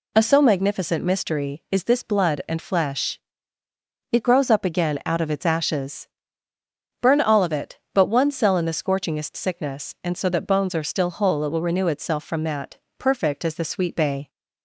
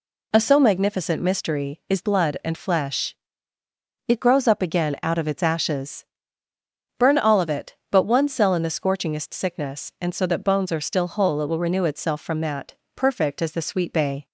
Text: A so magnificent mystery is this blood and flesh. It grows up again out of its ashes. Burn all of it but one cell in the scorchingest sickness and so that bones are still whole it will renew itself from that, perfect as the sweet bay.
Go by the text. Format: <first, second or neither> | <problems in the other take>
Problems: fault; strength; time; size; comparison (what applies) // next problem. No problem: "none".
first | skips "this"; at 2.0 s